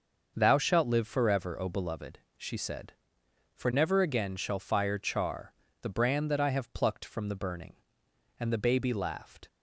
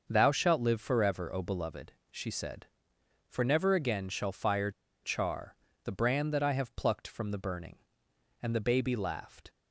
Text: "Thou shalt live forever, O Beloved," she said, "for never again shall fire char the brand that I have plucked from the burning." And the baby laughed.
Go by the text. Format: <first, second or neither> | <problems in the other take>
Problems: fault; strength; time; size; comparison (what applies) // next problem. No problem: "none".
first | starts louder than the rest; until 1.1 s; 6 dB; also in the first // pauses between "fire" and "char"; slight; at 4.6 s; 0.32 s long // pauses between "char" and "the"; slight; at 5.5 s; 0.28 s long; slight in the first